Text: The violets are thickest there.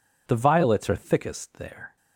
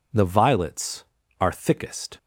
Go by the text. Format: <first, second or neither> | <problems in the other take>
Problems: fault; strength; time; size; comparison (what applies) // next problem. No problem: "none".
first | stops before "there"; at 2.1 s